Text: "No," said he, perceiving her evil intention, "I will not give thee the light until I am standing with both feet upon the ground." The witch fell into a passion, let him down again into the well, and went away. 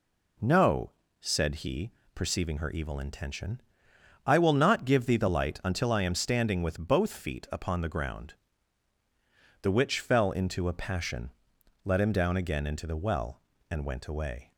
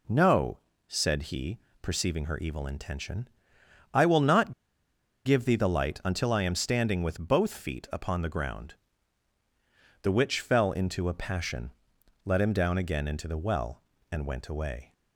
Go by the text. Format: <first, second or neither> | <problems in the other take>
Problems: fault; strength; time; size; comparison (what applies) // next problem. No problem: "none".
first | pauses between "not" and "give"; noticeable; at 4.5 s; 0.72 s long